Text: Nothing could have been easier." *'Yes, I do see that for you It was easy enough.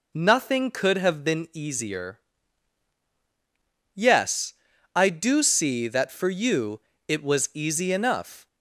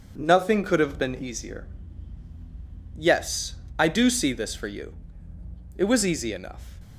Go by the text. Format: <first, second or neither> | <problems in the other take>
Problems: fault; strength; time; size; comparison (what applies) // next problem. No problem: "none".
first | says "this" for "that"; at 4.3 s // pauses between "you" and "It"; noticeable; at 4.9 s; 0.82 s long; slight in the first